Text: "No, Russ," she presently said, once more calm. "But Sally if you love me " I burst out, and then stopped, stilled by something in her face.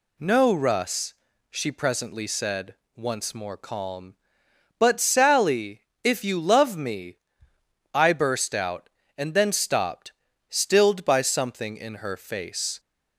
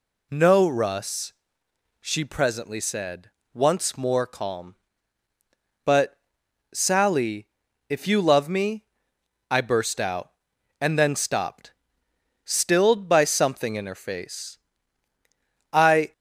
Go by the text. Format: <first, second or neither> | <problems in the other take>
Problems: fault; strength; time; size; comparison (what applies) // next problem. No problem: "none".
first | pauses between "But" and "Sally"; noticeable; at 6.1 s; 0.56 s long // pauses between "Sally" and "if"; at 7.4 s; 0.42 s long; slight in the first // goes on to say "I"; slight; from 15.7 s on; 0.40 s long